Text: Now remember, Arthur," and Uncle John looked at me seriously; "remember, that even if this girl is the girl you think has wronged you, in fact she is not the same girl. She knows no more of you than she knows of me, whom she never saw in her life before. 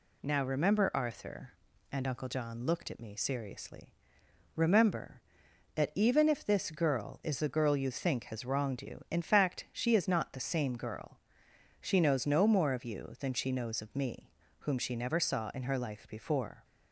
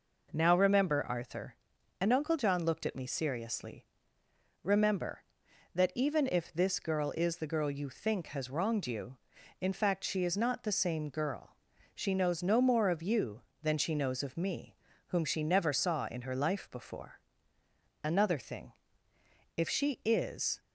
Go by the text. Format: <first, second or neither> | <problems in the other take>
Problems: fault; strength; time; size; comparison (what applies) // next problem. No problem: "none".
first | goes on to say "Another thing if she is"; strong; from 18.0 s on; 2.5 s long